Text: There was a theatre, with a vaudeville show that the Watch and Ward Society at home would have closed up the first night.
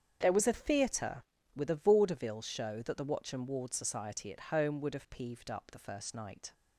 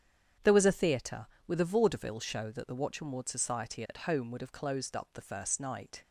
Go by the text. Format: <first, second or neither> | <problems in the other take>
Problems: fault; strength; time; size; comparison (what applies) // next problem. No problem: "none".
second | starts louder than the rest; strong; until 1.2 s; 8 dB; strong in the second // says "peeved" for "closed"; at 5.0 s